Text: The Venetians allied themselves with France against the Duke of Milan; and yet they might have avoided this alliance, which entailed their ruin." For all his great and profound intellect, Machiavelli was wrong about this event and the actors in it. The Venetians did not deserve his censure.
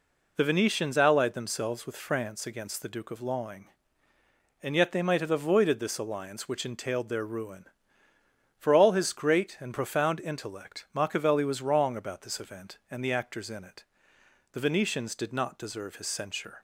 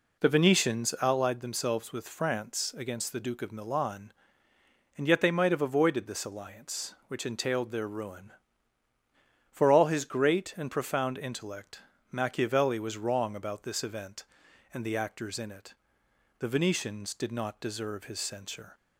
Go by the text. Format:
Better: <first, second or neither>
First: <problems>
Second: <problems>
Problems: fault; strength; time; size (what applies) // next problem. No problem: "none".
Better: second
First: says "Lawing" for "Milan"; at 3.2 s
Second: none